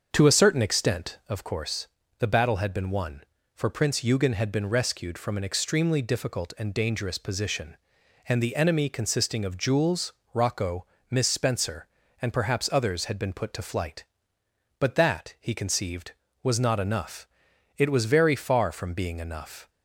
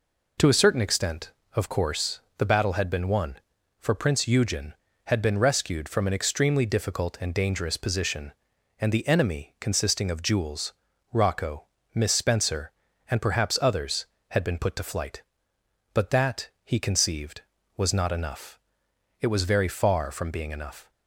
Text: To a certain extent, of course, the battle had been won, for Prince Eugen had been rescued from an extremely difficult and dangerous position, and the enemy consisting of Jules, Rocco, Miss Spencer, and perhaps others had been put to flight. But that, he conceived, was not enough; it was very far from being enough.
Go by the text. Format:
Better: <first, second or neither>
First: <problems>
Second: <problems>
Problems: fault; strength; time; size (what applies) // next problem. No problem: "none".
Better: second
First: starts louder than the rest; until 1.4 s; 7 dB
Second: none